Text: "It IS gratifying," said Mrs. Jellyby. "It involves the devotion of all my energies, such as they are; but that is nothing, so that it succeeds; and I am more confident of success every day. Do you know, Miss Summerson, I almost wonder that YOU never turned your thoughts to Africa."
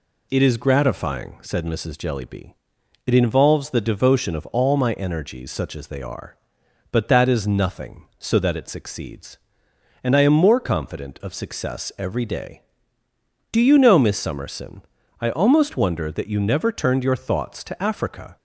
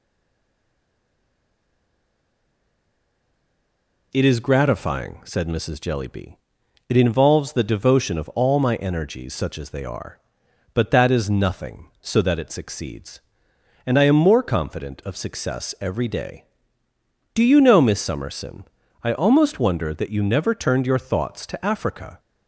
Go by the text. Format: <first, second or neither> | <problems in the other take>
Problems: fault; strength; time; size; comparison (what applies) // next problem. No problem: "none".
first | stays silent before the first word; strong; until 4.1 s; 4.1 s long